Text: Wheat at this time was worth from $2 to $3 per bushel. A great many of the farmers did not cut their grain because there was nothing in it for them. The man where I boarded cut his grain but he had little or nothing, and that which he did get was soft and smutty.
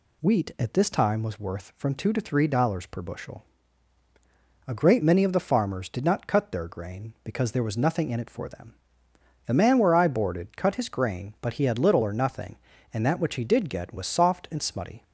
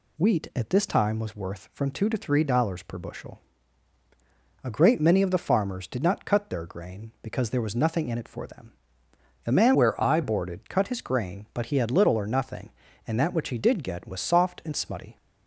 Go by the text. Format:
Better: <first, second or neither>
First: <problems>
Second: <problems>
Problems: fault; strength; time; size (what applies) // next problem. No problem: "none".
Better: first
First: none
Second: changes voice from "where" to "I"; from 9.7 to 10.2 s; 0.5 s long